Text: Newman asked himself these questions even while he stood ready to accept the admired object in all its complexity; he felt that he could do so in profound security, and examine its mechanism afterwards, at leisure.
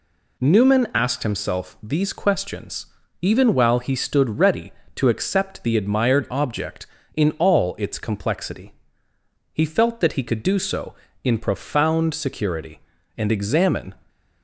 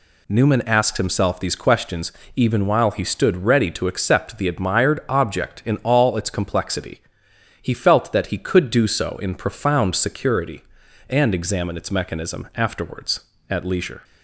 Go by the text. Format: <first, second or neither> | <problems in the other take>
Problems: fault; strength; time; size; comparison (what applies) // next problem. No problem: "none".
second | pauses between "questions" and "even"; slight; at 2.8 s; 0.34 s long; slight in the second // stops before "its mechanism afterwards at leisure"; at 14.0 s